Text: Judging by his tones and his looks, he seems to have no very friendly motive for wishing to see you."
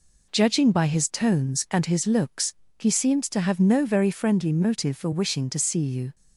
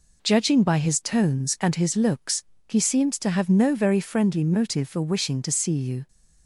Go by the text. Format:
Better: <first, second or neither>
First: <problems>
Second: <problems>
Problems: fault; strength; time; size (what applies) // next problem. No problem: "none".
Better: neither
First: none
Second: none